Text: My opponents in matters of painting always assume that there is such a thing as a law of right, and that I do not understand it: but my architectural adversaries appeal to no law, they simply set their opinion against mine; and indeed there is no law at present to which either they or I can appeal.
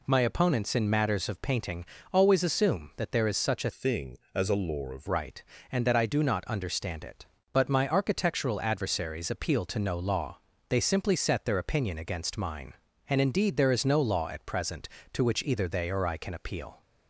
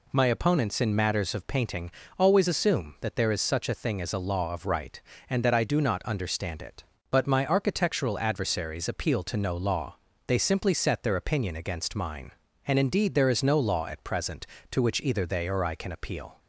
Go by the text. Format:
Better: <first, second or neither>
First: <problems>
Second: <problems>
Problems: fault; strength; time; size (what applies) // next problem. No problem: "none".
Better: second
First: pauses between "painting" and "always"; slight; at 1.8 s; 0.28 s long // changes voice from "thing" to "of"; from 3.7 to 5.0 s; 1.3 s long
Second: pauses between "painting" and "always"; slight; at 1.8 s; 0.28 s long